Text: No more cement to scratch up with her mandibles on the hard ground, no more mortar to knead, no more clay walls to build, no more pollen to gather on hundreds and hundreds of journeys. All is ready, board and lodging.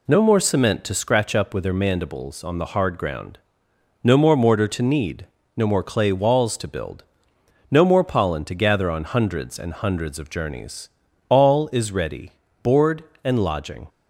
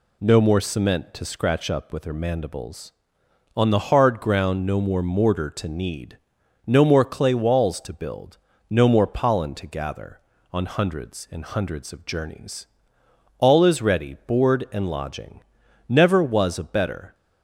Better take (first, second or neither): first